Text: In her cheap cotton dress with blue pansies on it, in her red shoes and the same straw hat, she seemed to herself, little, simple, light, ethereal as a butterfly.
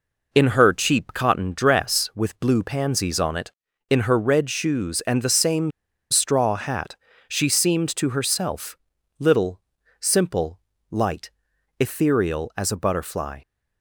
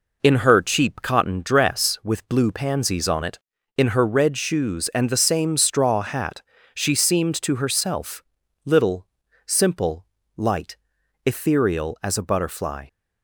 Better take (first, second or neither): second